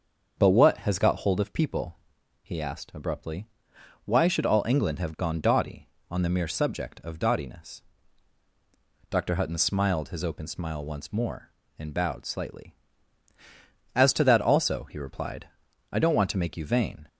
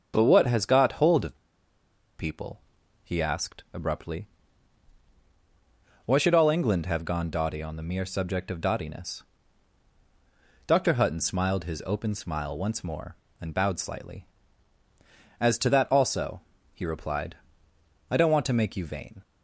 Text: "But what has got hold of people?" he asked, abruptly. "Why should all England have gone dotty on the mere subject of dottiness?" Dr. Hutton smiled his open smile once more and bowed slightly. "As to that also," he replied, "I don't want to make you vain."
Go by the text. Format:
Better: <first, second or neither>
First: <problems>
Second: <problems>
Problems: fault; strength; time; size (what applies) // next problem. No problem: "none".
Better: first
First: starts louder than the rest; until 1.3 s; 6.5 dB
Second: starts louder than the rest; until 1.1 s; 7 dB // pauses between "of" and "people"; noticeable; at 1.3 s; 0.84 s long